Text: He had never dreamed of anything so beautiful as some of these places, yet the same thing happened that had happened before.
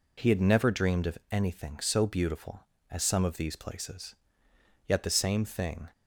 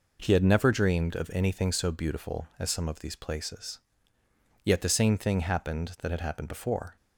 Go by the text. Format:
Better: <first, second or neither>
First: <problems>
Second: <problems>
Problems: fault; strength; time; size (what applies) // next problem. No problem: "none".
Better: second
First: stops before "happened that had happened before"; at 5.9 s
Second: none